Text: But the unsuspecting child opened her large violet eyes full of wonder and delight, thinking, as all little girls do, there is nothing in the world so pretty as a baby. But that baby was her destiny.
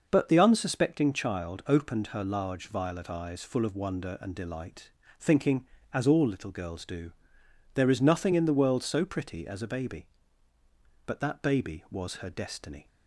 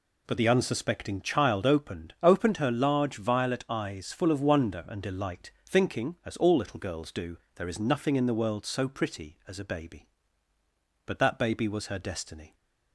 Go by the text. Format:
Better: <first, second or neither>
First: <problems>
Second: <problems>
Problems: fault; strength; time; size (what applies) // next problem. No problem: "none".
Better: first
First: none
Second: says "opened" twice; at 2.2 s